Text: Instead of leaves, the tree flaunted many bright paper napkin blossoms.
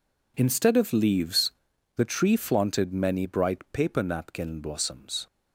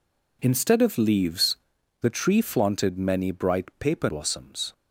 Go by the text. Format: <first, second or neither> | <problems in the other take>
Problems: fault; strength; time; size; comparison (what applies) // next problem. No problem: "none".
first | skips "napkin"; at 4.0 s